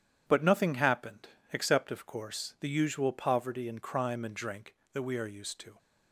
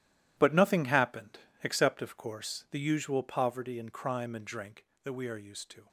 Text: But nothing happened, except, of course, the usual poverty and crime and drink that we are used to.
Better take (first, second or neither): first